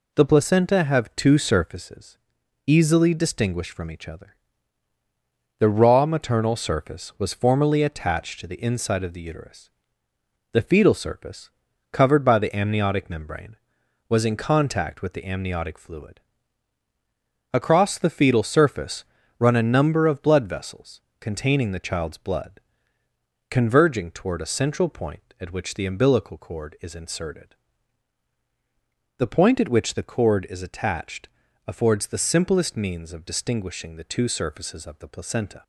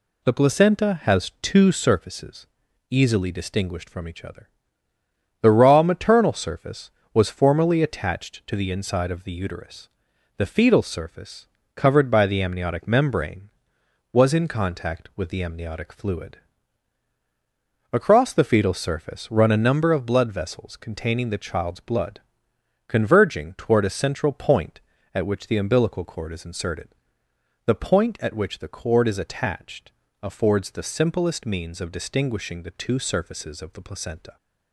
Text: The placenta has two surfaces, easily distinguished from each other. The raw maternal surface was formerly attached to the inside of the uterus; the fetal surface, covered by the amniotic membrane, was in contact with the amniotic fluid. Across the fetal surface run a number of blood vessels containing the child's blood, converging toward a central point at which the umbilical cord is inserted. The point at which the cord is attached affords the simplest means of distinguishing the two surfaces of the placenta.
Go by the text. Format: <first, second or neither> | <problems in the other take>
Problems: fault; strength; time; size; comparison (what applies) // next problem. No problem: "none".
second | says "have" for "has"; at 0.8 s // pauses between "surface" and "run"; slight; at 19.0 s; 0.34 s long // pauses between "vessels" and "containing"; slight; at 21.0 s; 0.20 s long // pauses between "attached" and "affords"; slight; at 31.2 s; 0.36 s long; slight in the second